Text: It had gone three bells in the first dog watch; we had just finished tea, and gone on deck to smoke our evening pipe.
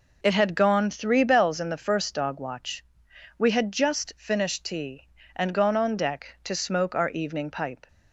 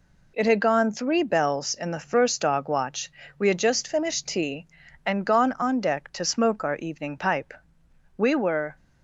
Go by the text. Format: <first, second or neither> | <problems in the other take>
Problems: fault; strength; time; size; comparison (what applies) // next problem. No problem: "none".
first | goes on to say "We were"; from 8.1 s on; 0.58 s long